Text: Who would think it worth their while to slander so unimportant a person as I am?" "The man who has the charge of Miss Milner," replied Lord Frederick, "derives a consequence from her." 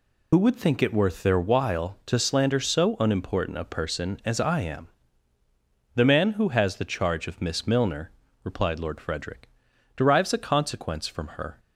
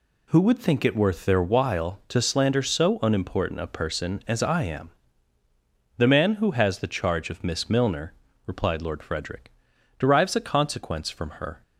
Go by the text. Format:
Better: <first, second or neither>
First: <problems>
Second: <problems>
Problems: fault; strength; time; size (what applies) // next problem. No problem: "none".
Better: second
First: loses the start of "Who"; at 0.3 s; 55 ms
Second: none